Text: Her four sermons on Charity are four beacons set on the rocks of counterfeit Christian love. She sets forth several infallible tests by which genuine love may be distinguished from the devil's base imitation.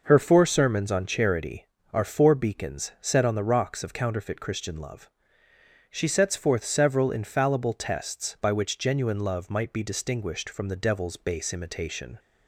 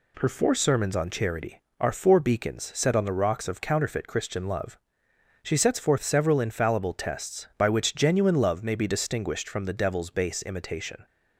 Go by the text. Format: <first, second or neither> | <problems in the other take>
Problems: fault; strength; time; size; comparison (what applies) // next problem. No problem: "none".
second | says "might" for "may"; at 9.4 s